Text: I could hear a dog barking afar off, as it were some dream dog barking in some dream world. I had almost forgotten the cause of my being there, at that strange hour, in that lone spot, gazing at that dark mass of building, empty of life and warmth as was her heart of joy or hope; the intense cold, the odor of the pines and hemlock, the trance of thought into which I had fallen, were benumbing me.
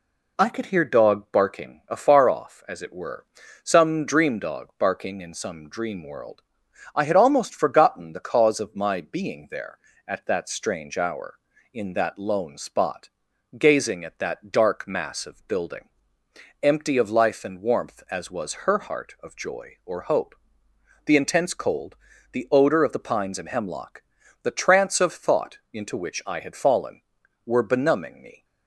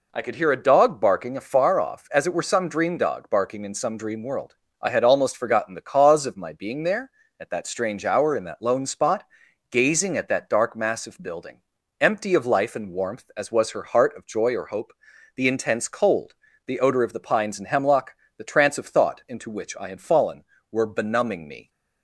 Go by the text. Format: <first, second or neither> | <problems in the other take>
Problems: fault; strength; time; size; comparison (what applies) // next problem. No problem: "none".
second | skips "a"; at 0.8 s // pauses between "were" and "some"; at 3.2 s; 0.40 s long